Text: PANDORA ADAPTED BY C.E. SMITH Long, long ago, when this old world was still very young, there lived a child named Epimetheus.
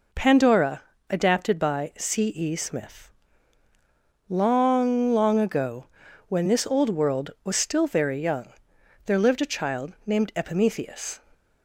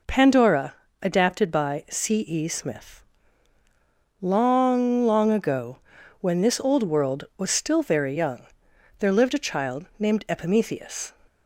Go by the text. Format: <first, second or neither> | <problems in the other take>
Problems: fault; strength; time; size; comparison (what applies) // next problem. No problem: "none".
neither | pauses between "PANDORA" and "ADAPTED"; slight; the same in both // pauses between "SMITH" and "Long"; the same in both